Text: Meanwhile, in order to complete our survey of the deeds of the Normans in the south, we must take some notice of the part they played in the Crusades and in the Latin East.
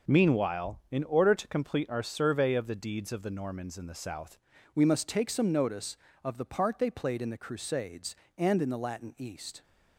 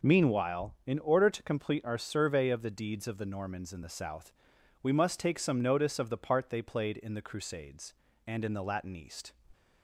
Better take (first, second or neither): second